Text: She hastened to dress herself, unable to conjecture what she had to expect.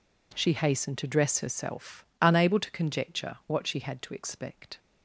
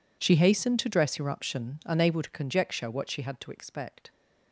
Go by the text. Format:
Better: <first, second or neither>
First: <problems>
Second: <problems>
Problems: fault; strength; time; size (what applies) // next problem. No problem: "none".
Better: first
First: none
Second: says "eruption" for "herself"; at 1.2 s